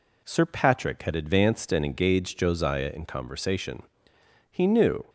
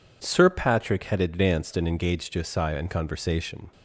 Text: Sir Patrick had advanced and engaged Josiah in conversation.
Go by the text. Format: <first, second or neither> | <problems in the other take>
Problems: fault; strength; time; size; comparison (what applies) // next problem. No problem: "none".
second | goes on to say "He knew"; from 4.5 s on; 0.54 s long